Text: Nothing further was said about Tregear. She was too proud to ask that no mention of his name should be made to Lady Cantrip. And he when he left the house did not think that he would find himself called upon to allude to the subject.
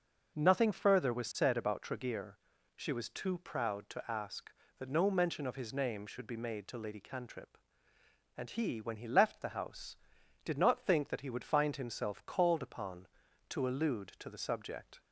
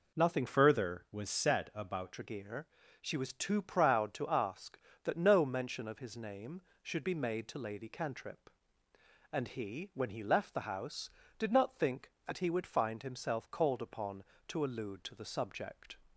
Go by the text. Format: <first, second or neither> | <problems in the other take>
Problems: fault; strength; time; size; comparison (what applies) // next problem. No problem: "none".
first | changes voice from "further" to "about"; from 0.4 to 2.1 s; 1.7 s long